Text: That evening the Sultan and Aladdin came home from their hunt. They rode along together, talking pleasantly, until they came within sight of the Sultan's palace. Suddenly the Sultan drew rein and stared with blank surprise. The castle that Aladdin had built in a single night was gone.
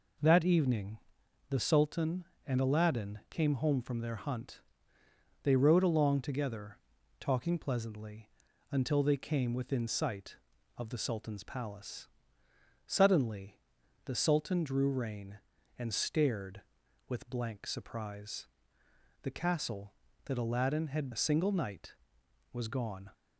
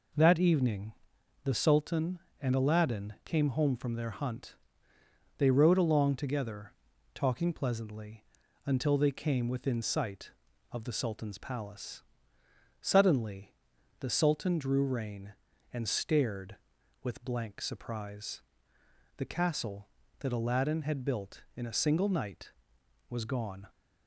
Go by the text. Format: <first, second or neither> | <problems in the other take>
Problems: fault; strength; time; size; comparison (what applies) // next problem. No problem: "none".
second | pauses between "evening" and "the"; noticeable; at 0.9 s; 0.52 s long; noticeable in the second // pauses between "Suddenly" and "the"; noticeable; at 13.5 s; 0.46 s long; noticeable in the second // skips "built in"; at 21.1 s